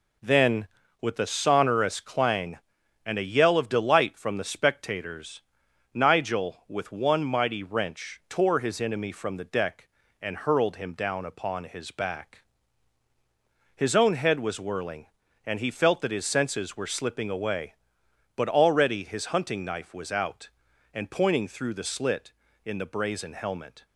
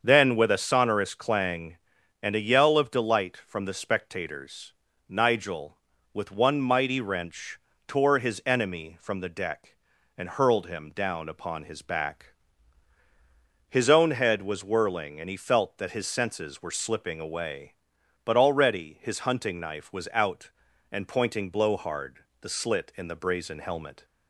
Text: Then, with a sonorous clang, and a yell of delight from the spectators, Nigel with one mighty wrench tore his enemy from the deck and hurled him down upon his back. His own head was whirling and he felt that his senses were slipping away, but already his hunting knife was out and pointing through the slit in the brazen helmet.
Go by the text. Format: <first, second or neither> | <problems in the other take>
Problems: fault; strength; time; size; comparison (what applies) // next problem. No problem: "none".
first | starts louder than the rest; until 1.0 s; 7 dB // pauses between "wrench" and "tore"; slight; at 7.5 s; 0.30 s long // says "blowhard" for "through"; at 21.4 s